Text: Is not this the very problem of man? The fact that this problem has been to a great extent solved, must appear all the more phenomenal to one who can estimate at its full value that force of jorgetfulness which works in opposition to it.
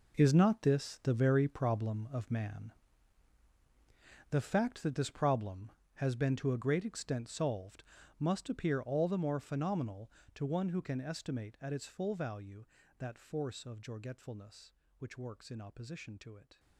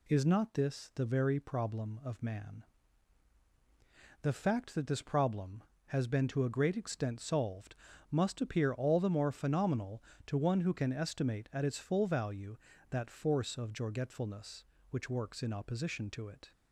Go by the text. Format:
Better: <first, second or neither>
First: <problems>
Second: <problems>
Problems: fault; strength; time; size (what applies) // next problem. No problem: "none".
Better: second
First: gets quieter; strong; throughout; 14 dB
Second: none